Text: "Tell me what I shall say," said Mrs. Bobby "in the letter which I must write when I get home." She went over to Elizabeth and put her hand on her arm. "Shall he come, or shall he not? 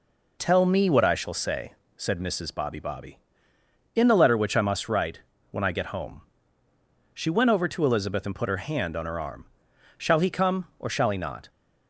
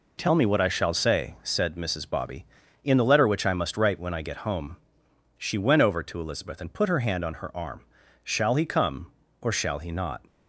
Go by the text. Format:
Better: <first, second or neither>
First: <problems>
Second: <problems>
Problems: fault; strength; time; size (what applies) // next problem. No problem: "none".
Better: second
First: says "Bobby" twice; at 2.7 s // pauses between "write" and "when"; slight; at 5.2 s; 0.30 s long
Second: none